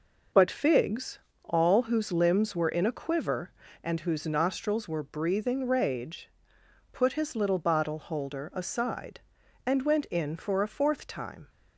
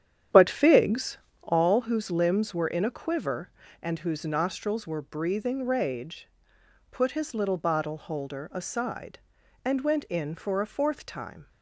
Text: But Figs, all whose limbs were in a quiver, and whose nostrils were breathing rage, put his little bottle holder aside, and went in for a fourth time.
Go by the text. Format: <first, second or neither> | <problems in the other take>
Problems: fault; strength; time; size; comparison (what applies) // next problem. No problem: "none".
first | starts louder than the rest; strong; until 1.7 s; 9.5 dB